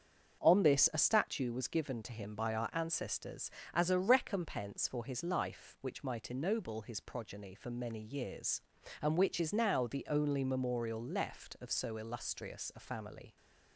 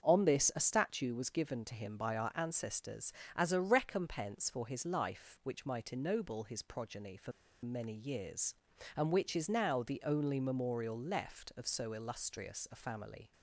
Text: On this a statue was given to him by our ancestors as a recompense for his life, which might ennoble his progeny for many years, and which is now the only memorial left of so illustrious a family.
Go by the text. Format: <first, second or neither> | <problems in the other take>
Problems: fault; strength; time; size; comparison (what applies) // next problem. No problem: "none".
first | starts louder than the rest; until 1.0 s; 7 dB; also in the first // pauses between "for" and "many"; slight; at 7.3 s; 0.32 s long